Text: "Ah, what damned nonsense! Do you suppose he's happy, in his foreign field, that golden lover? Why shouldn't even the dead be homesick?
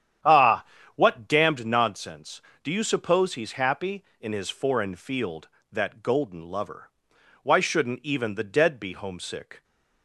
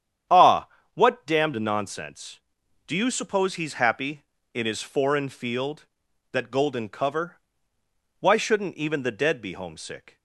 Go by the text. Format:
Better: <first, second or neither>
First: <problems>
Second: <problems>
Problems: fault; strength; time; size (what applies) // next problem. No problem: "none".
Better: first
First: starts louder than the rest; strong; until 1.5 s; 9.5 dB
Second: starts louder than the rest; strong; until 1.5 s; 9 dB // says "cover" for "lover"; at 6.8 s